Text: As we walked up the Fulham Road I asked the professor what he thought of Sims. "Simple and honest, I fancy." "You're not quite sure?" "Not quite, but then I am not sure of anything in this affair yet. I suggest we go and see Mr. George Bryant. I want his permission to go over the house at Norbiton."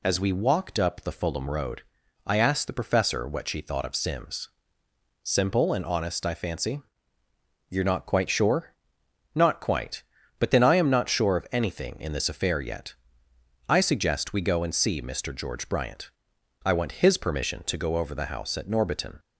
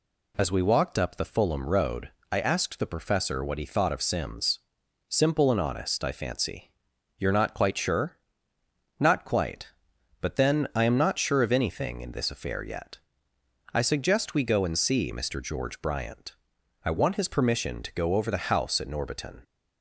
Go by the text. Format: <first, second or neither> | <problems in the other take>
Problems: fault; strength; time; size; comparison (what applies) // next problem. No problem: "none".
second | pauses between "Road" and "I"; at 1.8 s; 0.42 s long; slight in the second // says "she" for "he"; at 3.4 s